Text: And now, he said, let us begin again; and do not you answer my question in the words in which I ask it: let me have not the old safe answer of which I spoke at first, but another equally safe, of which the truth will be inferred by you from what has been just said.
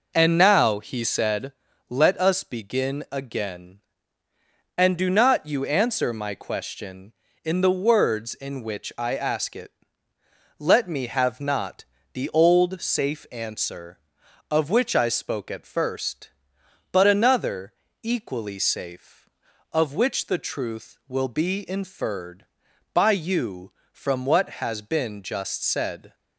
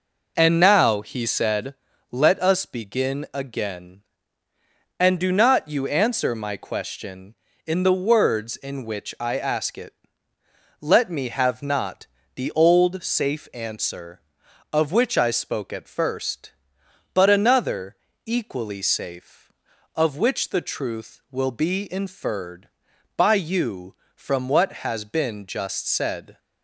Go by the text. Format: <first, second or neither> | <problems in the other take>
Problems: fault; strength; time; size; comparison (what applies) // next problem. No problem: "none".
neither | pauses between "not" and "the"; slight; the same in both // pauses between "another" and "equally"; slight; the same in both